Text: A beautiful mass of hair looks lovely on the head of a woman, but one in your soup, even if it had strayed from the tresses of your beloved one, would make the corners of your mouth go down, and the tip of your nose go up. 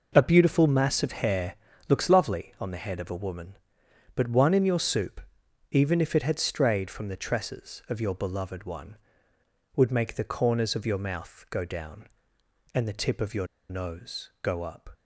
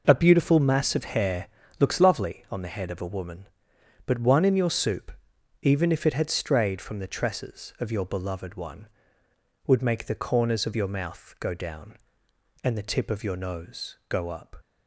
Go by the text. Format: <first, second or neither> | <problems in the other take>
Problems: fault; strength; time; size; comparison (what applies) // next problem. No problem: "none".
second | pauses between "hair" and "looks"; slight; at 1.5 s; 0.34 s long; slight in the second // pauses between "your" and "nose"; slight; at 13.4 s; 0.23 s long